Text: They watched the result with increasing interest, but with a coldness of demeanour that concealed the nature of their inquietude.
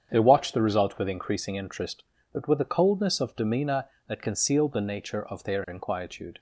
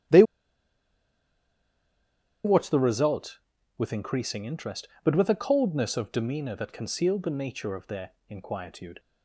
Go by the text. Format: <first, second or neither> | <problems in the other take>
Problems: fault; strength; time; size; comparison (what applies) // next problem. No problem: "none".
first | starts louder than the rest; strong; until 3.3 s; 11.5 dB; strong in the first // pauses between "They" and "watched"; strong; at 0.2 s; 2.2 s long // pauses between "their" and "inquietude"; slight; at 8.1 s; 0.18 s long